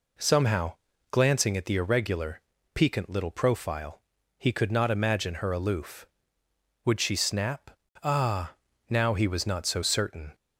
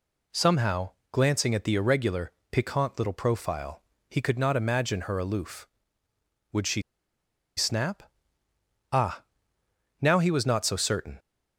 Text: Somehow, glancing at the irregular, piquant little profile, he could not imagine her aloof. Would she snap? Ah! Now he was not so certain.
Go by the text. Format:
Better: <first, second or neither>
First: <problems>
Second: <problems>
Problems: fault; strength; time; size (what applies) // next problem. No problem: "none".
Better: first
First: none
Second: pauses between "she" and "snap"; noticeable; at 6.8 s; 0.74 s long